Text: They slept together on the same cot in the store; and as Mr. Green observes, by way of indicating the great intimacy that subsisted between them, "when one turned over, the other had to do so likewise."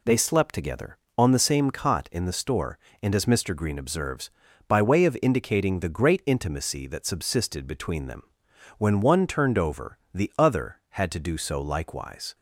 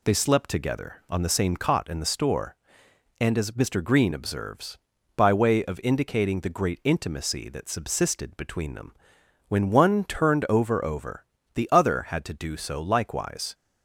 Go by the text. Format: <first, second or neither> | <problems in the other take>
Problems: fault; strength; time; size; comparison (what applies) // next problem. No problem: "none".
first | says "over" twice; at 10.8 s